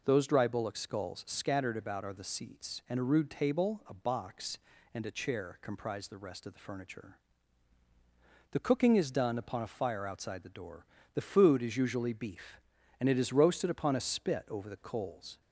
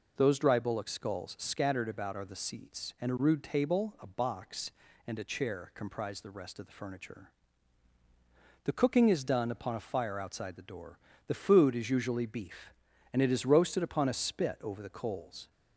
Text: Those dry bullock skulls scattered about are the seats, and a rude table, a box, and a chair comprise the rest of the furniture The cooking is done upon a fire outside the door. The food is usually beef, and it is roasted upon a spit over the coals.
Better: neither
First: pauses between "furniture" and "The"; strong; at 7.1 s; 1.3 s long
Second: pauses between "furniture" and "The"; strong; at 7.2 s; 1.3 s long

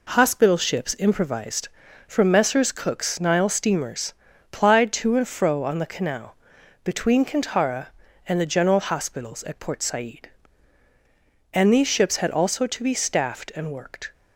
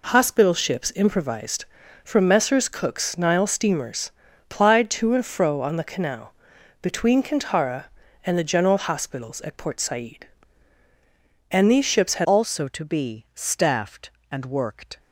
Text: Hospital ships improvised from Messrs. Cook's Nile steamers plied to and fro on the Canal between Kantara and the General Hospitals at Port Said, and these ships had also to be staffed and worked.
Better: first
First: pauses between "steamers" and "plied"; at 4.1 s; 0.40 s long // pauses between "Canal" and "between"; noticeable; at 6.3 s; 0.52 s long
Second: pauses between "steamers" and "plied"; at 4.1 s; 0.40 s long // pauses between "Canal" and "between"; noticeable; at 6.3 s; 0.52 s long // changes voice at "also"; from 12.2 s on; 2.7 s long

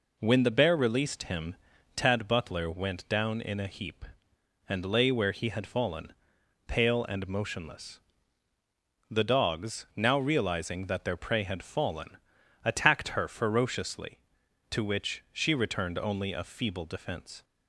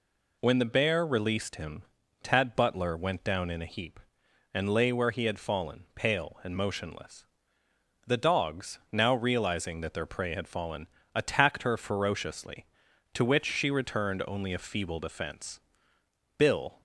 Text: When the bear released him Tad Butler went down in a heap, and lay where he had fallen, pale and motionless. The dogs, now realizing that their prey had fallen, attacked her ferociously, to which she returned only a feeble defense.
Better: first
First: pauses between "him" and "Tad"; at 1.5 s; 0.40 s long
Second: pauses between "him" and "Tad"; at 1.8 s; 0.40 s long // goes on to say "Bill"; slight; from 16.3 s on; 0.44 s long

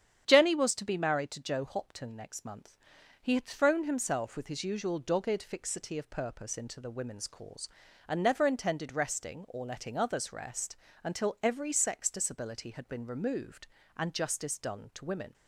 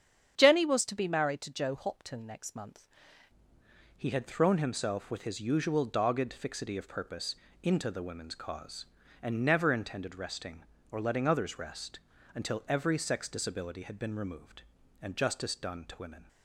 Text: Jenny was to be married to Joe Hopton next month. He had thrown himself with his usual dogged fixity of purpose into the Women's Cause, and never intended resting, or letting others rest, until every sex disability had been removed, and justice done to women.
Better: first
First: starts louder than the rest; strong; until 1.2 s; 9 dB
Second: starts louder than the rest; strong; until 1.4 s; 8.5 dB // changes voice at "He"; from 3.9 s on; 12.3 s long // pauses between "purpose" and "into"; slight; at 7.3 s; 0.30 s long

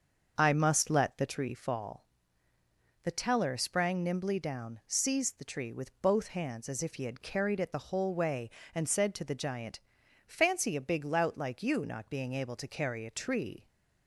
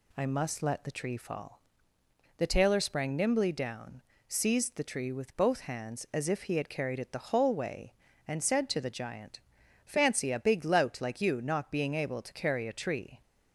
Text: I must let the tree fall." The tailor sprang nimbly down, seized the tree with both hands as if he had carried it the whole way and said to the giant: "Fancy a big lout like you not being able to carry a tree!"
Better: second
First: starts louder than the rest; until 1.3 s; 6.5 dB // says "teller" for "tailor"; at 3.1 s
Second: none

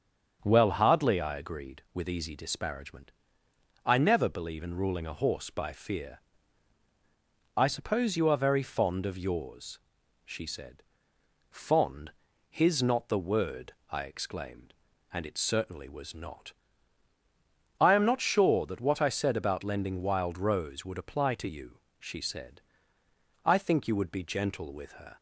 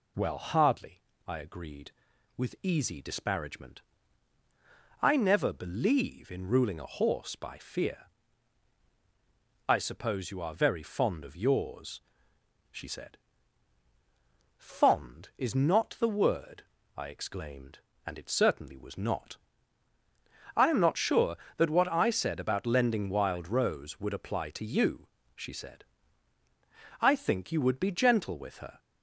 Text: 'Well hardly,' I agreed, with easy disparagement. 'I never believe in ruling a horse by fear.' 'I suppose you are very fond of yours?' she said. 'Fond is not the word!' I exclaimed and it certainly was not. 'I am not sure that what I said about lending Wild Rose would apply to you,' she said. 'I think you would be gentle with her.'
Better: second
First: starts louder than the rest; until 1.4 s; 7 dB // says "his" for "is"; at 12.4 s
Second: none

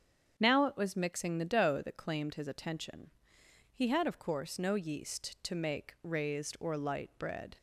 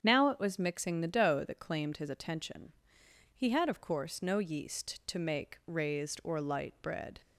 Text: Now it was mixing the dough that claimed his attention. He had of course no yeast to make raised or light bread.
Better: neither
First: starts louder than the rest; strong; until 1.4 s; 8 dB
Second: starts louder than the rest; strong; until 1.0 s; 8 dB

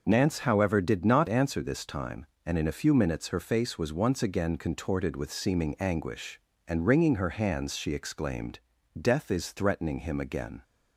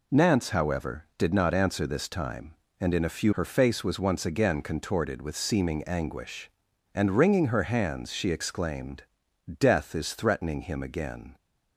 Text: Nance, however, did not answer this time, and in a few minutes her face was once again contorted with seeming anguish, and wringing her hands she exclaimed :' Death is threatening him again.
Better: first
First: none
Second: skips "minutes"; at 3.3 s

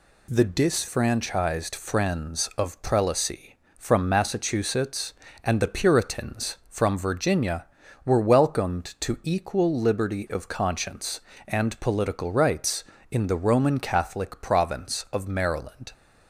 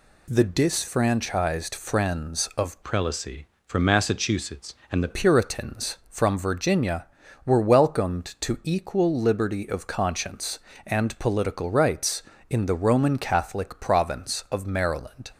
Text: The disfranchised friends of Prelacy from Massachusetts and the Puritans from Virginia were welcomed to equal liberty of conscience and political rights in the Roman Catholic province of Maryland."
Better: first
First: none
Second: changes voice from "Prelacy" to "the"; from 2.8 to 5.0 s; 2.2 s long

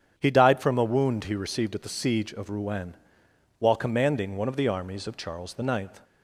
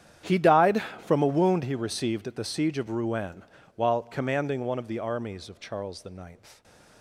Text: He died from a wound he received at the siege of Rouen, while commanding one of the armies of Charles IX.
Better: first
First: starts louder than the rest; strong; until 1.1 s; 8.5 dB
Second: gets quieter; strong; throughout; 19 dB // starts louder than the rest; strong; until 1.4 s; 10 dB // stays silent after the last word; slight; from 6.3 s on; 0.7 s long

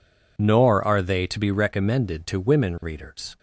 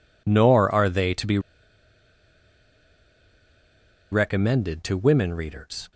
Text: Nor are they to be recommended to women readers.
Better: first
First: none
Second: pauses between "be" and "recommended"; strong; at 1.3 s; 2.7 s long

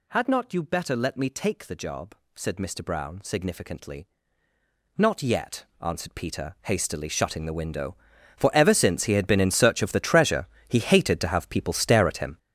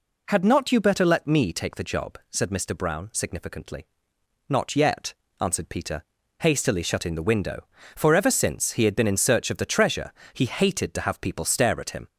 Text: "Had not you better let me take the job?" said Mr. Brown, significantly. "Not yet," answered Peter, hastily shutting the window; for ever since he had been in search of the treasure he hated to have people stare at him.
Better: second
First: gets louder; strong; throughout; 10 dB // pauses between "treasure" and "he"; slight; at 10.4 s; 0.22 s long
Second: pauses between "treasure" and "he"; slight; at 10.1 s; 0.18 s long

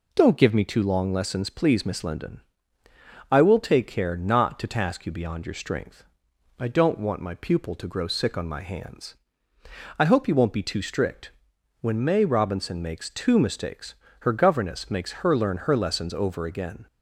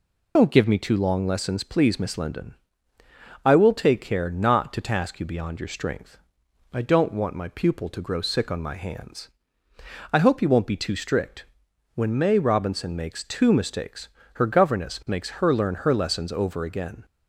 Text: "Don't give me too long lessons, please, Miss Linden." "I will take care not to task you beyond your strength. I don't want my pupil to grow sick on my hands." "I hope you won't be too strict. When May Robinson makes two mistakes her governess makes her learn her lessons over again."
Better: first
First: pauses between "mistakes" and "her"; slight; at 13.9 s; 0.26 s long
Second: loses the start of "Don't"; at 0.3 s; 80 ms // pauses between "mistakes" and "her"; slight; at 14.0 s; 0.26 s long

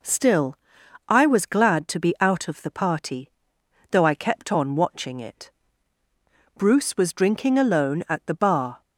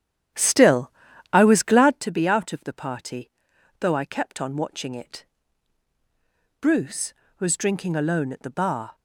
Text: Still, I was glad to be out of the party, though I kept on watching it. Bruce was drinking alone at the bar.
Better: first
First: none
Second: starts louder than the rest; strong; until 2.1 s; 10.5 dB

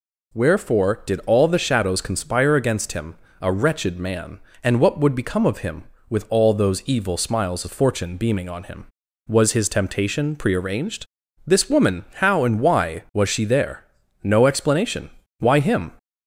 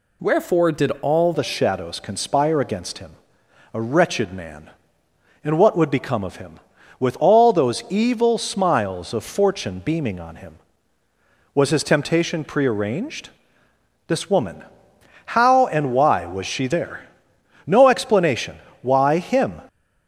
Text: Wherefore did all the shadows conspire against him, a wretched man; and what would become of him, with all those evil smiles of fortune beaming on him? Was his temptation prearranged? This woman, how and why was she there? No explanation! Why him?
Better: first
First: none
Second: changes voice at "the"; from 1.3 s on; 18.2 s long

